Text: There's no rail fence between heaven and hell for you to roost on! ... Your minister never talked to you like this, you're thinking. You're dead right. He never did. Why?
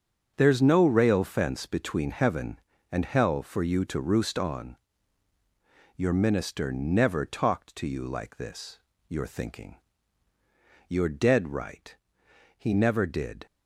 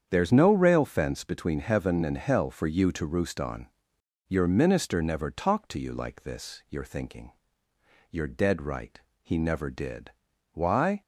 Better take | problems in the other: second | starts louder than the rest; strong; until 1.3 s; 7 dB; strong in the second // stops before "Why"; at 13.4 s

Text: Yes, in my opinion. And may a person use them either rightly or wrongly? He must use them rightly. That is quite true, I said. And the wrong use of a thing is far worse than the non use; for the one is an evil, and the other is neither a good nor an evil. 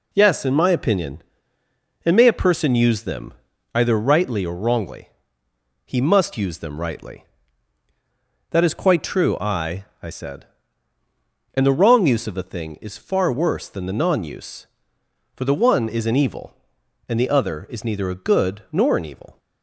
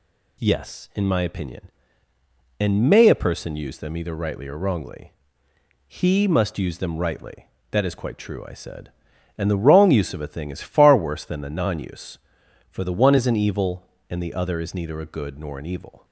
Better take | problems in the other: second | pauses between "them" and "either"; at 3.3 s; 0.40 s long // says "I" twice; at 10.0 s

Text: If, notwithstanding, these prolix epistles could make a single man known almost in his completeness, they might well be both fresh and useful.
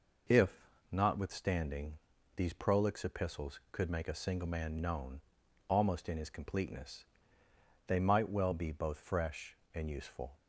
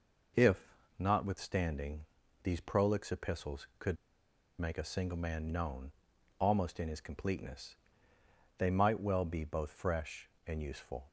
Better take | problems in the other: first | pauses between "could" and "make"; noticeable; at 3.9 s; 0.63 s long // pauses between "known" and "almost"; noticeable; at 5.9 s; 0.48 s long; noticeable in the first

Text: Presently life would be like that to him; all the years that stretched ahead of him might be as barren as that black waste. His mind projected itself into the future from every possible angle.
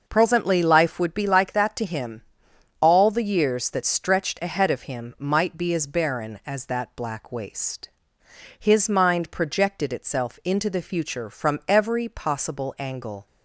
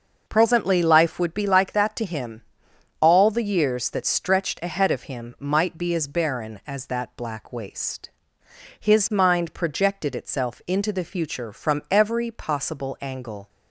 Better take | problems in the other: neither | starts louder than the rest; noticeable; the same in both

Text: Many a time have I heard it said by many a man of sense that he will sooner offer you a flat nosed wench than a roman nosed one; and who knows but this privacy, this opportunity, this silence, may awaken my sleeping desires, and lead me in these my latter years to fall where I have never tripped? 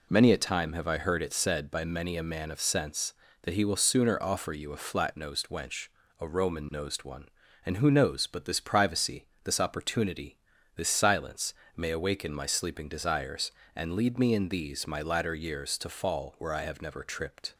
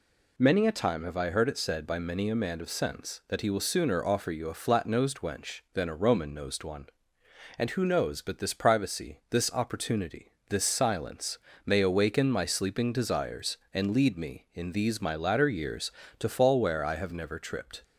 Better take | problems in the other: second | skips "than"; at 6.0 s

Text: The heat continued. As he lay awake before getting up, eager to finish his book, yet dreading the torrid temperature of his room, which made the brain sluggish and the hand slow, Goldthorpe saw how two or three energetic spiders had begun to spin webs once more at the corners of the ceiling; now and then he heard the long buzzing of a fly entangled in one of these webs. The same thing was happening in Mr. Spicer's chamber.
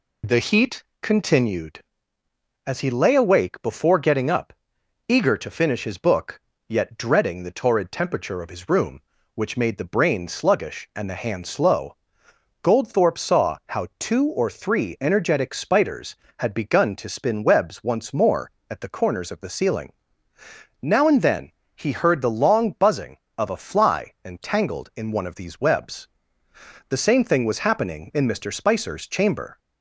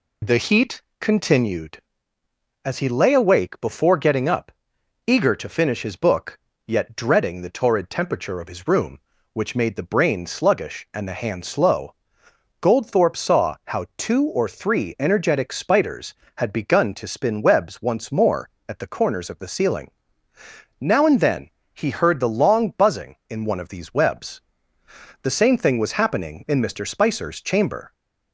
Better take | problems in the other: first | pauses between "heat" and "continued"; slight; at 0.8 s; 0.20 s long; slight in the first // pauses between "then" and "he"; slight; at 21.4 s; 0.24 s long; slight in the first // skips "of a fly entangled"; at 23.2 s

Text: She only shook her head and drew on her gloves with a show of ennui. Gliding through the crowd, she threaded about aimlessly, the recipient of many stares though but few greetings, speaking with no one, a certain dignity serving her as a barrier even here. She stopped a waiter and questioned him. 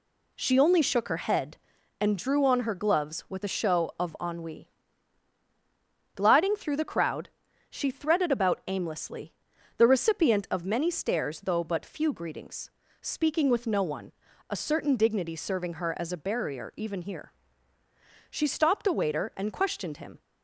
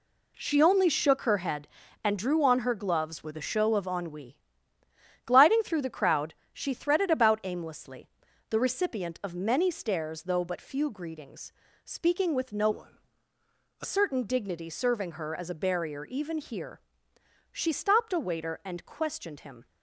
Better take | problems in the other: first | changes voice from "one" to "a"; from 12.7 to 13.8 s; 1.1 s long

